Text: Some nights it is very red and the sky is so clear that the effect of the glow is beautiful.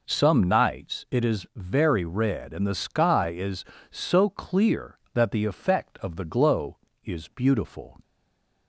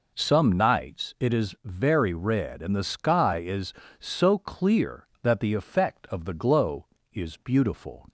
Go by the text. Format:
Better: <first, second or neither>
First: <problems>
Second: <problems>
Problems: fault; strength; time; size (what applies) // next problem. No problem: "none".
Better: second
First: stays silent after the last word; slight; from 8.0 s on; 0.6 s long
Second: none